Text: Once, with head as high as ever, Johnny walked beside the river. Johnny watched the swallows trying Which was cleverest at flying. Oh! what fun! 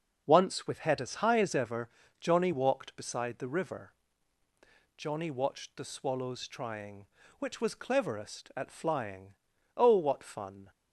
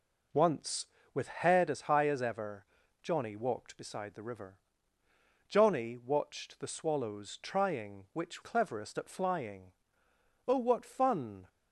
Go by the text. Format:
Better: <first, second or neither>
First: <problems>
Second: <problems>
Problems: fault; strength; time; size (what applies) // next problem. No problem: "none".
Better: first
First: none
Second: skips "was"; at 8.4 s